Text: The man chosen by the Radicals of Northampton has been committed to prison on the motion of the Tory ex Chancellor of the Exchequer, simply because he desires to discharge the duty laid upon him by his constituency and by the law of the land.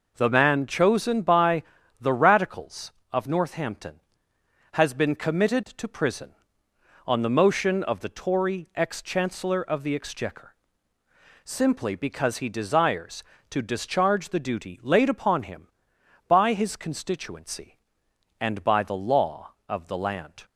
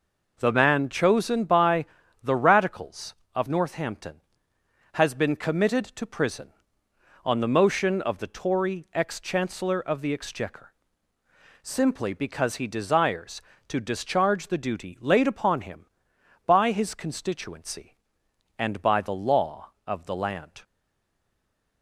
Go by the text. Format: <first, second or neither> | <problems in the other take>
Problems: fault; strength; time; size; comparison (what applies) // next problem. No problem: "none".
first | pauses between "by" and "the"; slight; at 1.8 s; 0.36 s long; slight in the first // stays silent after the last word; noticeable; from 20.6 s on; 1.2 s long